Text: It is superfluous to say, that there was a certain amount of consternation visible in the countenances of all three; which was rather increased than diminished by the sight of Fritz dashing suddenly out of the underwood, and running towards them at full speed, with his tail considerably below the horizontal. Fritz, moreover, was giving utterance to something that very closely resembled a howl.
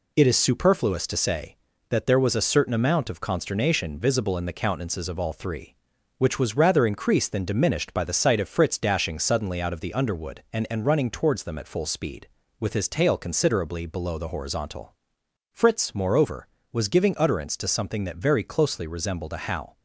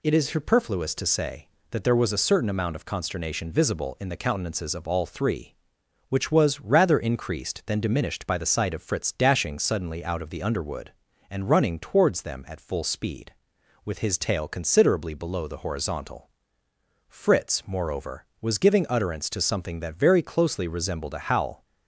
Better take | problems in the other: second | says "and" twice; at 10.6 s

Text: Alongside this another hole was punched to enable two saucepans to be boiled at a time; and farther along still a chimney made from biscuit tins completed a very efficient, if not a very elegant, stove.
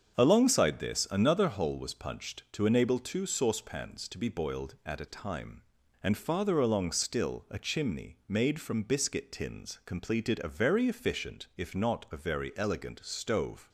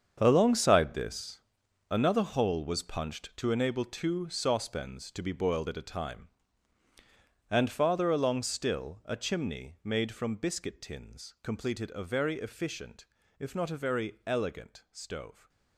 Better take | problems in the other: first | gets quieter; strong; throughout; 12 dB // starts louder than the rest; strong; until 1.2 s; 7.5 dB; strong in the first // pauses between "this" and "another"; noticeable; at 1.3 s; 0.50 s long

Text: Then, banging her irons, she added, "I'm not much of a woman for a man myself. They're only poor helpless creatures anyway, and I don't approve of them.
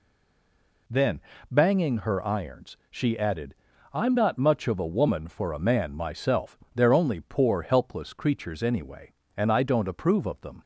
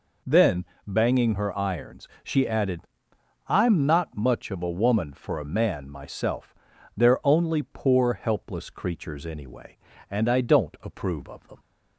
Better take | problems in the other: second | stays silent before the first word; slight; until 0.8 s; 0.8 s long

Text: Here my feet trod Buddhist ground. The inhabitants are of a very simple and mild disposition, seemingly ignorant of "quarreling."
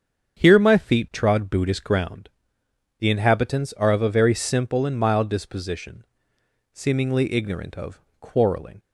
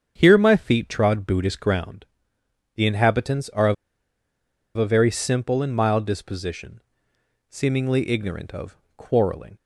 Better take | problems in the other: first | starts louder than the rest; strong; until 1.1 s; 7 dB; strong in the first // pauses between "of" and "a"; at 3.7 s; 1.0 s long // pauses between "of" and "quarreling"; slight; at 8.7 s; 0.22 s long; slight in the first

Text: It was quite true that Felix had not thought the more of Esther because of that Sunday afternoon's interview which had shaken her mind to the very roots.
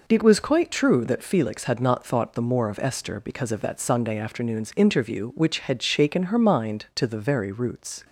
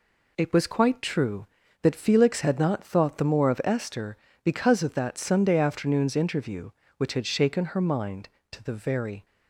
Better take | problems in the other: first | stops before "roots"; at 9.2 s

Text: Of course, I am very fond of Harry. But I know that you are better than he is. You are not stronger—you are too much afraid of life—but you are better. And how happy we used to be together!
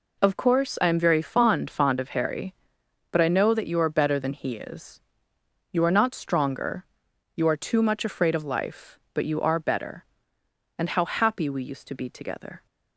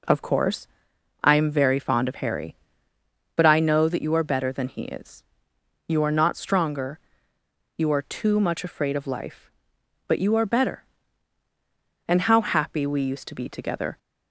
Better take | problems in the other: second | says "fond" twice; at 1.6 s

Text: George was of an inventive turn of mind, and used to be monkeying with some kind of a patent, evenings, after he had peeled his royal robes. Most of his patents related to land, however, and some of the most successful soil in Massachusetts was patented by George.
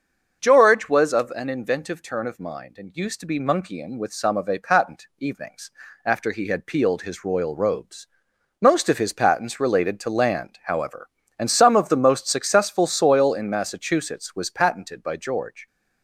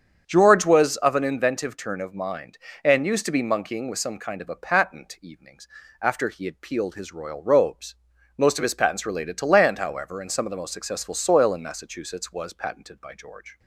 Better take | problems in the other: second | starts louder than the rest; until 1.4 s; 6.5 dB; strong in the second // skips "kind"; at 4.3 s

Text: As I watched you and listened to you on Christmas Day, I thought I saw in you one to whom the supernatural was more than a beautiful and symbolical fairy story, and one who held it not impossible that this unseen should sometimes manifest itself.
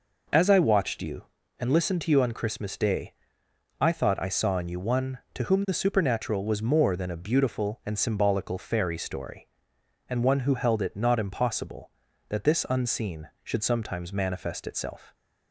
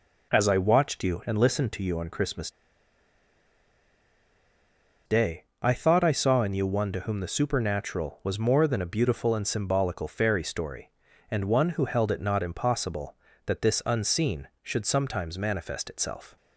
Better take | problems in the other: first | pauses between "Christmas" and "Day"; strong; at 2.5 s; 2.5 s long

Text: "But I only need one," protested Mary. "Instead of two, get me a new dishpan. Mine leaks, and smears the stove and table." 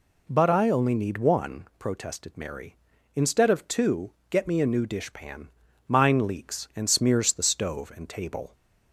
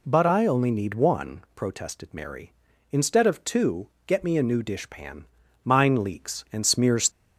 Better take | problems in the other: first | stops before "the stove and table"; at 7.1 s

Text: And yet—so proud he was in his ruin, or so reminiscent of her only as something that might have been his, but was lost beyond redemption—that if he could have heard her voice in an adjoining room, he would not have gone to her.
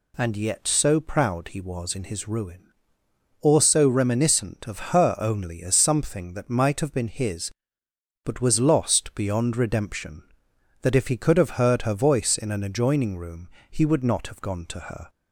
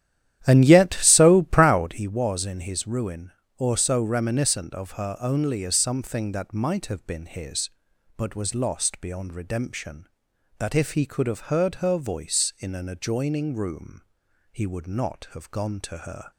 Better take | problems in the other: first | starts louder than the rest; strong; until 2.1 s; 11.5 dB

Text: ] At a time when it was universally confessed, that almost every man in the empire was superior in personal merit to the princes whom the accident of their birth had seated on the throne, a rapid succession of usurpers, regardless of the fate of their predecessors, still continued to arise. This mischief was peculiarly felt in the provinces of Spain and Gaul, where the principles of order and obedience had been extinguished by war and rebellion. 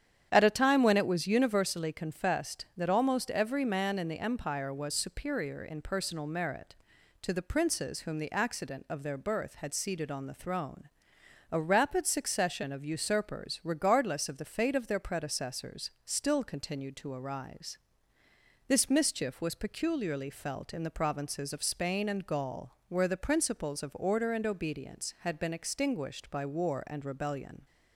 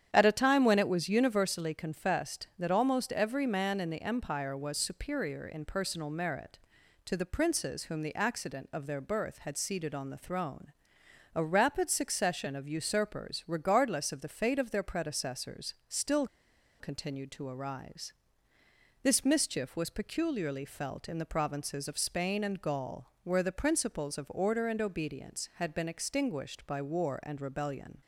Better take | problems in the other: first | starts louder than the rest; strong; until 1.1 s; 9.5 dB; strong in the first // pauses between "still" and "continued"; noticeable; at 16.2 s; 0.54 s long

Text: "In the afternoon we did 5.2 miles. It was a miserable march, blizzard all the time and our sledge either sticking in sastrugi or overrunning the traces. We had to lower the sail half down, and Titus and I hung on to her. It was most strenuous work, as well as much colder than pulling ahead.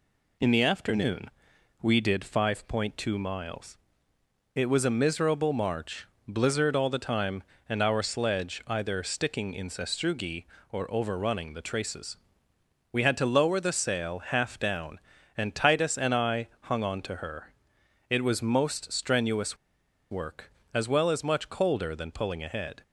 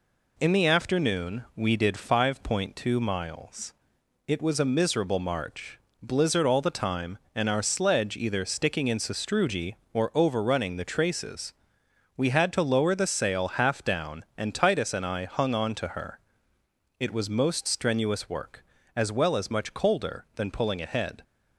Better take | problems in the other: second | pauses between "afternoon" and "we"; noticeable; at 1.2 s; 0.50 s long // pauses between "strenuous" and "work"; noticeable; at 19.5 s; 0.54 s long

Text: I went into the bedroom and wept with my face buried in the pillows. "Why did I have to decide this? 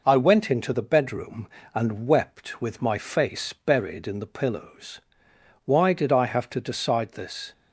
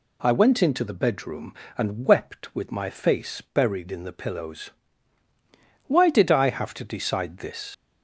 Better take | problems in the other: first | leaves "this" unfinished; at 7.7 s; 85 ms

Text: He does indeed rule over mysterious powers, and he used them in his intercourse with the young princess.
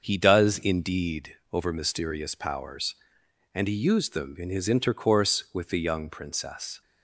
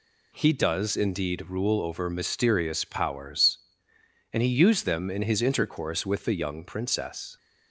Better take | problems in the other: second | starts louder than the rest; until 1.0 s; 6 dB // skips "rule"; at 1.4 s

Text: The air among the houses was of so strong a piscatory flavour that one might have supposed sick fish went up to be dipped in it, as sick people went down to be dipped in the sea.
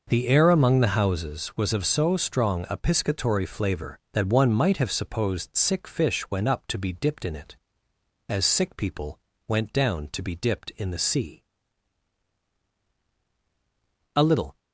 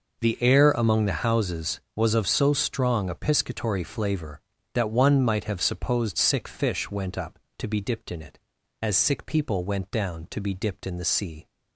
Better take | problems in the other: second | pauses between "people" and "went"; slight; at 9.1 s; 0.28 s long // goes on to say "A little"; slight; from 14.1 s on; 0.42 s long

